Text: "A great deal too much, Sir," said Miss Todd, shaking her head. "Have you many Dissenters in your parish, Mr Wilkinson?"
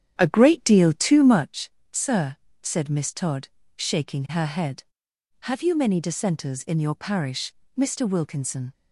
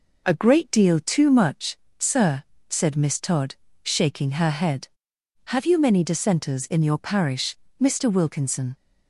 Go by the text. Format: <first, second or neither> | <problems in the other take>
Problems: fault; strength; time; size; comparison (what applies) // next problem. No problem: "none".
second | starts louder than the rest; strong; until 1.4 s; 9.5 dB